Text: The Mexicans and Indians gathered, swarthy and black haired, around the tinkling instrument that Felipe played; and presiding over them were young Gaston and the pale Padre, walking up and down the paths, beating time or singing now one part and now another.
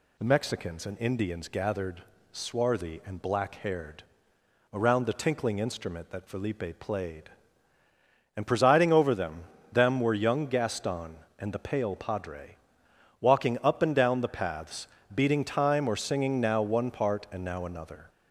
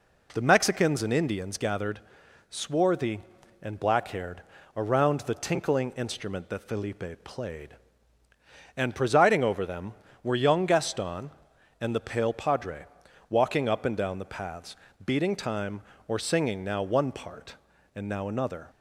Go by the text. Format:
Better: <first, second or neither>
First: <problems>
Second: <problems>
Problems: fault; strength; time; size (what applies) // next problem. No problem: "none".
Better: second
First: says "them" twice; at 9.7 s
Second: none